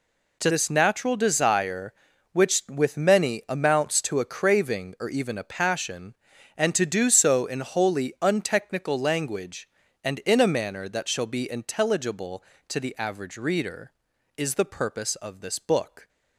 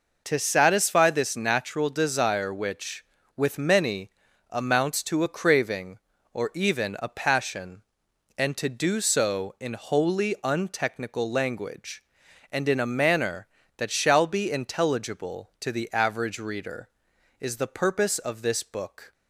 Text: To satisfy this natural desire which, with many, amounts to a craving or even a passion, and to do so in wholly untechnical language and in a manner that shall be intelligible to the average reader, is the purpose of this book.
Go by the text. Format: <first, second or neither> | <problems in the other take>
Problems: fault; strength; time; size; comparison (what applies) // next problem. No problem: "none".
second | skips "satisfy"; at 0.4 s